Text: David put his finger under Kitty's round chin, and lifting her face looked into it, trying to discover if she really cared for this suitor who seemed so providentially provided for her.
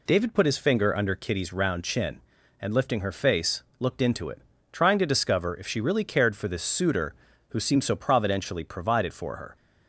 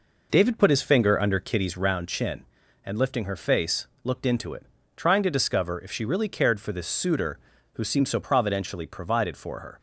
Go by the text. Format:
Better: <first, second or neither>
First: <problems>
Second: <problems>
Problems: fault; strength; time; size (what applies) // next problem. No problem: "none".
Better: first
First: pauses between "face" and "looked"; slight; at 3.6 s; 0.18 s long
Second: starts louder than the rest; noticeable; until 2.0 s; 4.5 dB // pauses between "face" and "looked"; slight; at 3.8 s; 0.18 s long